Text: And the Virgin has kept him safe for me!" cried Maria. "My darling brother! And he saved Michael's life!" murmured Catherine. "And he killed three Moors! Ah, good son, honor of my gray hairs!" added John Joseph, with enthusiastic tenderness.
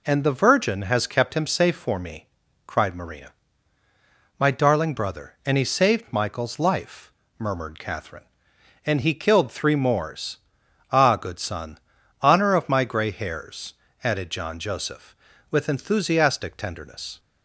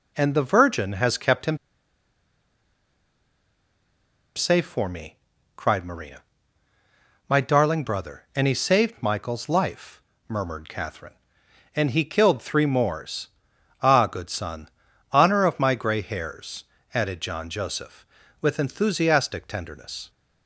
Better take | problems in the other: first | pauses between "him" and "safe"; strong; at 1.5 s; 2.7 s long

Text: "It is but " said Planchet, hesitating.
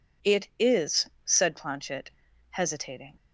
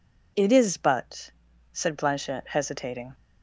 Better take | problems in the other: second | skips "but"; at 1.1 s

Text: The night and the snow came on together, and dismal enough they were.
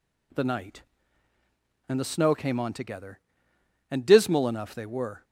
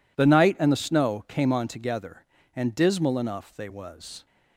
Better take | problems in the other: first | says "was" for "were"; at 3.6 s

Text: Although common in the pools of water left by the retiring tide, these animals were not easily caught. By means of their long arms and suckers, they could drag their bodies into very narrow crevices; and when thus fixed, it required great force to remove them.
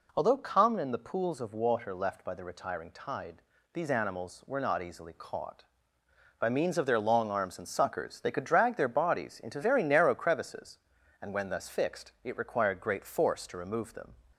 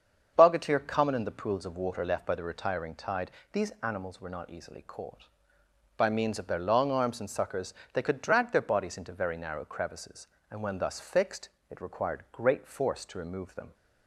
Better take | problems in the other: first | starts louder than the rest; until 1.3 s; 7 dB // says "Bogatir" for "Although"; at 0.3 s

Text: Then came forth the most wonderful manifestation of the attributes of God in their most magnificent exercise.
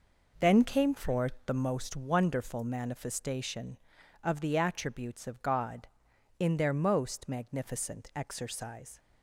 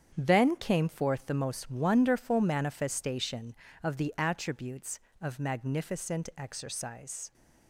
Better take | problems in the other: first | starts louder than the rest; strong; until 1.1 s; 8.5 dB // skips "God in their most"; at 5.3 s

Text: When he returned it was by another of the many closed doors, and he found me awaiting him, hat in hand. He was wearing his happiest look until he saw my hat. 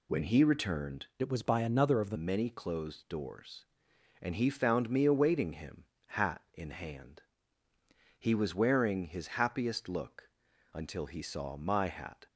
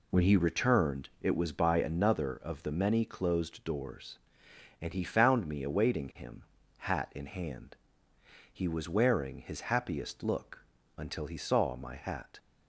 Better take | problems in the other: second | changes voice from "it" to "the"; from 1.2 to 2.1 s; 0.9 s long // pauses between "look" and "until"; at 10.2 s; 0.44 s long; slight in the second

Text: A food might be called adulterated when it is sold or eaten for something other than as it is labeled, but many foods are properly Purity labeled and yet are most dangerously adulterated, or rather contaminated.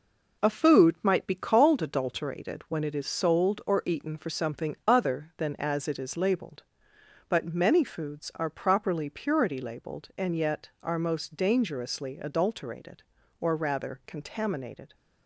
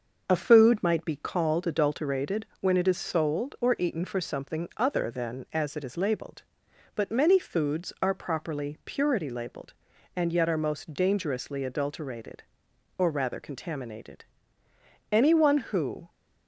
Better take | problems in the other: first | starts louder than the rest; noticeable; until 1.2 s; 6 dB // goes on to say "Anyone who"; noticeable; from 15.1 s on; 0.96 s long

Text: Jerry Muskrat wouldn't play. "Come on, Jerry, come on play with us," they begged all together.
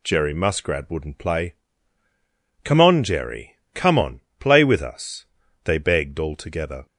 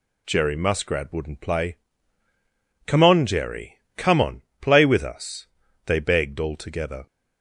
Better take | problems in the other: neither | pauses between "on" and "play"; slight; the same in both

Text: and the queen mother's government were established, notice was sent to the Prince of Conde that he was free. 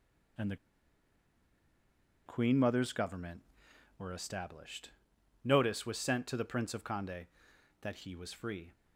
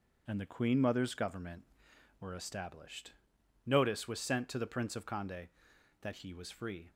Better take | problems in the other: second | pauses between "the" and "queen"; strong; at 0.5 s; 1.7 s long

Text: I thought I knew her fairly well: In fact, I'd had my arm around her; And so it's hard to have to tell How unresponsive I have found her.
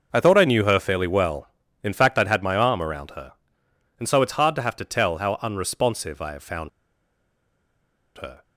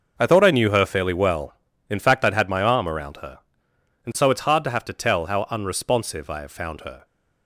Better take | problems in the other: second | starts louder than the rest; noticeable; until 1.1 s; 6 dB; also in the second // pauses between "found" and "her"; strong; at 6.6 s; 1.4 s long

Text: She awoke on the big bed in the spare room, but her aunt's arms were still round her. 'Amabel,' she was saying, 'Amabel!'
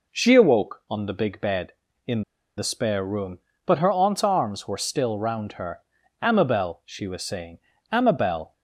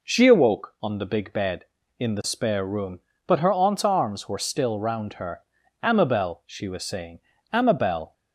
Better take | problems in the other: second | pauses between "in" and "the"; slight; at 2.2 s; 0.34 s long

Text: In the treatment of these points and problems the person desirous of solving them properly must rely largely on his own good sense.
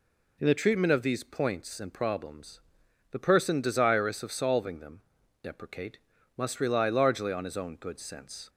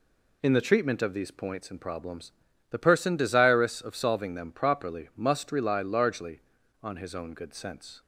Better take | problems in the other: second | pauses between "problems" and "the"; noticeable; at 2.5 s; 0.50 s long; also in the second // says "deprecate" for "properly"; at 5.4 s

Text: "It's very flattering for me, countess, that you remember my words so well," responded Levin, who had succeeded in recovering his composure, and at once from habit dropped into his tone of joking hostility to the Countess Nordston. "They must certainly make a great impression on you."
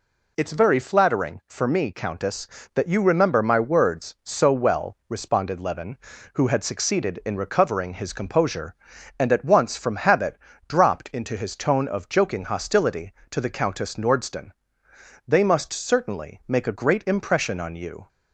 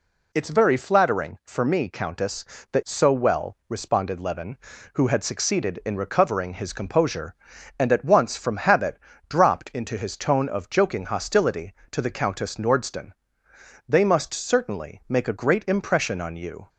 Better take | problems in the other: first | skips "you remember my words"; at 2.8 s // pauses between "habit" and "dropped"; slight; at 8.9 s; 0.30 s long; slight in the first

